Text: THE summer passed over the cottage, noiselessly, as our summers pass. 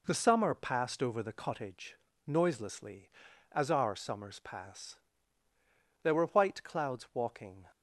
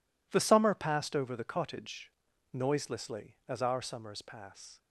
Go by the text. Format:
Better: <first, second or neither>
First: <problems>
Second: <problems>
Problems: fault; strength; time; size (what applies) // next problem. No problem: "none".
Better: second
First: goes on to say "There were white clouds walking"; from 6.0 s on; 1.6 s long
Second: none